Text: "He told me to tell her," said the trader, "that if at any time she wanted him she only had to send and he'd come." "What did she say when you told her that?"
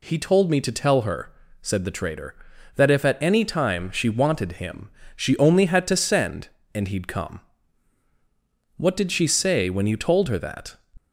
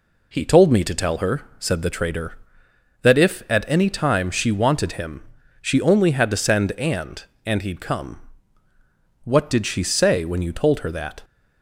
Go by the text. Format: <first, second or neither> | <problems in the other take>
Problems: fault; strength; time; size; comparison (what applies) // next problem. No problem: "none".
first | pauses between "him" and "she"; at 5.1 s; 0.40 s long; slight in the first // says "and" twice; at 7.4 s